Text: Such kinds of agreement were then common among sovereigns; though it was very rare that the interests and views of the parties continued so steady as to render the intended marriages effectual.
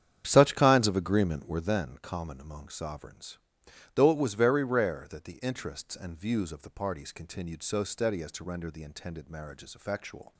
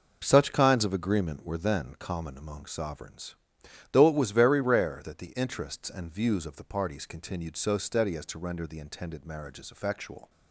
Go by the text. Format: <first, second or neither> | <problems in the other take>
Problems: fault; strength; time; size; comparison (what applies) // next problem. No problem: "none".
second | starts louder than the rest; strong; until 1.8 s; 9 dB